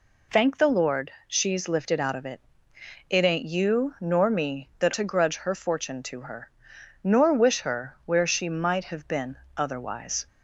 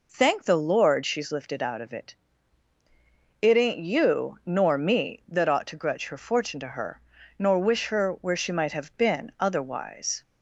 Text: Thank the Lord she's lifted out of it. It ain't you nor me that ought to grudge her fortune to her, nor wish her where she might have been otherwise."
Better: second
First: pauses between "Lord" and "she's"; slight; at 1.0 s; 0.16 s long // skips "ought"; at 4.9 s // pauses between "been" and "otherwise"; slight; at 9.3 s; 0.18 s long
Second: none

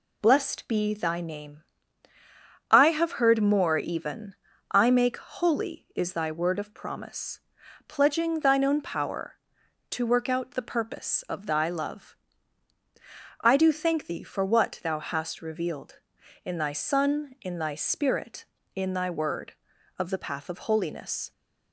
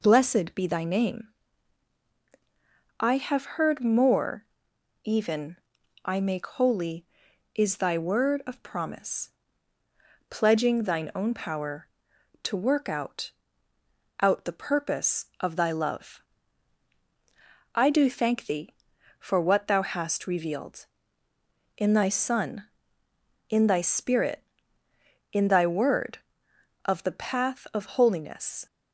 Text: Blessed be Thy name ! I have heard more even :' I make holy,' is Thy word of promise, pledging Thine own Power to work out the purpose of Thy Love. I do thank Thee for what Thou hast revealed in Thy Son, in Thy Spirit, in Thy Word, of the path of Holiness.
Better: first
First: none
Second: pauses between "more" and "even"; noticeable; at 4.4 s; 0.58 s long // says "out" twice; at 14.1 s

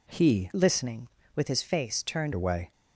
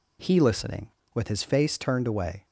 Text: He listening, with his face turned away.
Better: second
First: changes voice from "listening" to "turned"; from 0.5 to 2.3 s; 1.8 s long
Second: none

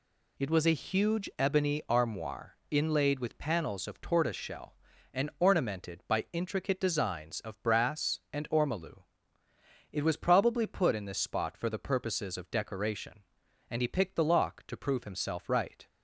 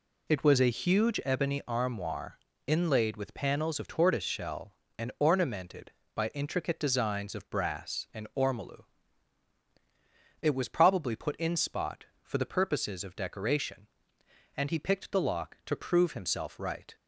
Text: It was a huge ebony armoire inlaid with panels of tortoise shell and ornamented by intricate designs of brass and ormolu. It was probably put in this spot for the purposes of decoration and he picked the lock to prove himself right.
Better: first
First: none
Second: pauses between "armoire" and "inlaid"; slight; at 2.3 s; 0.28 s long // skips "this"; at 11.5 s

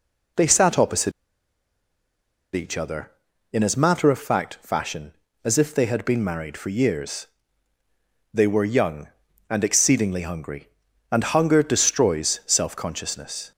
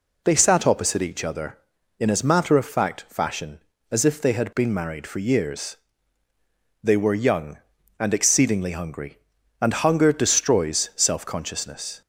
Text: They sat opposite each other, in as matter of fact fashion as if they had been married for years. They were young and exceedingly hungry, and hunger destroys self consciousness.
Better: second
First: pauses between "opposite" and "each"; strong; at 1.1 s; 1.4 s long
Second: none

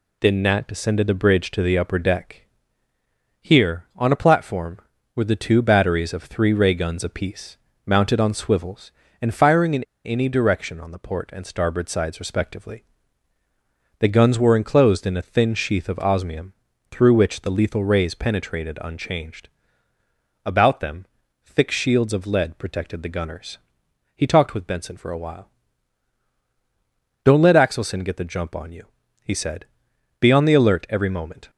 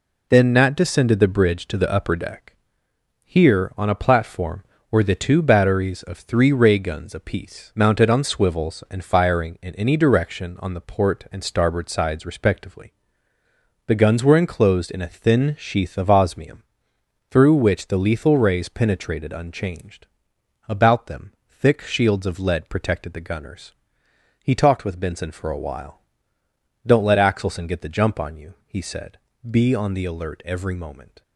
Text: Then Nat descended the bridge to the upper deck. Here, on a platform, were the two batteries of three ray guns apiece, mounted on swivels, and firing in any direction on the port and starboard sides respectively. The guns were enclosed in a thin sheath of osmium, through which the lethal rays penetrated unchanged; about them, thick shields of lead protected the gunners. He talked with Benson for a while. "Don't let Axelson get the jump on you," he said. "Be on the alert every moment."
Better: second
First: pauses between "in" and "any"; slight; at 9.8 s; 0.22 s long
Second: none

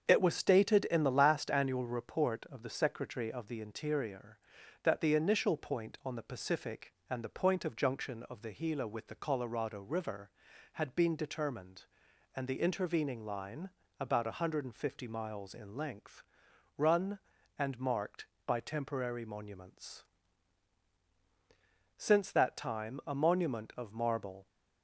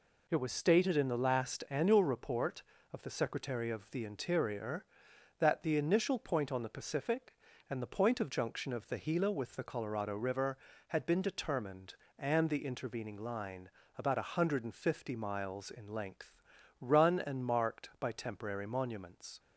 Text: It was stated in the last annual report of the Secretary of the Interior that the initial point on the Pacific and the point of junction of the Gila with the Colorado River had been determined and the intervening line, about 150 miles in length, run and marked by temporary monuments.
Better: second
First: starts louder than the rest; until 1.0 s; 7 dB // goes on to say "Since that time a monument of marble"; strong; from 21.9 s on; 2.4 s long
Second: none

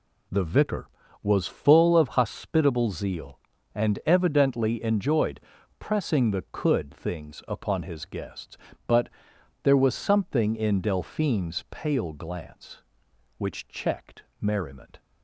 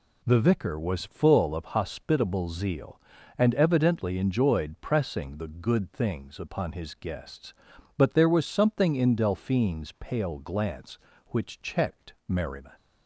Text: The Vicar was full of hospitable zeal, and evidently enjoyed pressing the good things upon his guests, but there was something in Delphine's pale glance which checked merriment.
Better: second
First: pauses between "enjoyed" and "pressing"; at 5.4 s; 0.38 s long // says "could" for "good"; at 6.5 s // pauses between "but" and "there"; noticeable; at 9.0 s; 0.54 s long // pauses between "checked" and "merriment"; slight; at 14.2 s; 0.16 s long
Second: pauses between "checked" and "merriment"; slight; at 12.1 s; 0.16 s long

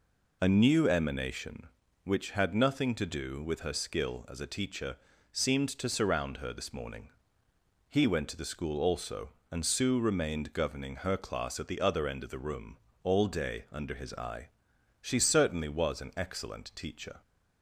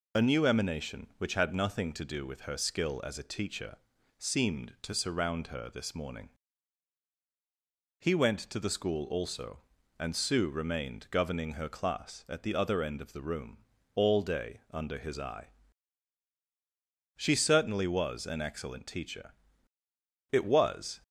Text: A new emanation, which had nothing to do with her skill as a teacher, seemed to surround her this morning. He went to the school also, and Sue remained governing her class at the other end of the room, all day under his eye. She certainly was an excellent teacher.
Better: first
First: none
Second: goes on to say "It was"; noticeable; from 20.3 s on; 0.70 s long

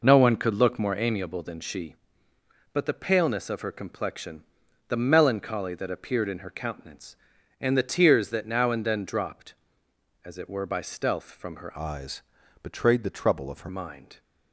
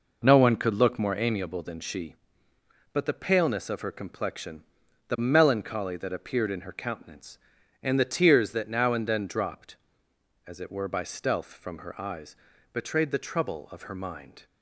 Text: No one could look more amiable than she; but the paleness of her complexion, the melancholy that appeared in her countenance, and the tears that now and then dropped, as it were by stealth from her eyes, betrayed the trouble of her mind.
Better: second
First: changes voice from "eyes" to "her"; from 11.7 to 13.6 s; 1.9 s long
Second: none

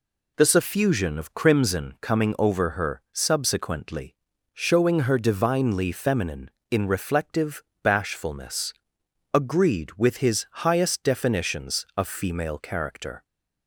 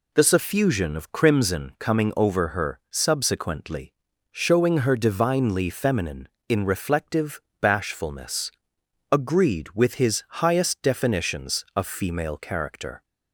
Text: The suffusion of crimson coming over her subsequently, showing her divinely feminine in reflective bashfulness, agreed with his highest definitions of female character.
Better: neither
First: pauses between "reflective" and "bashfulness"; slight; at 7.6 s; 0.20 s long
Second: pauses between "reflective" and "bashfulness"; slight; at 7.4 s; 0.20 s long

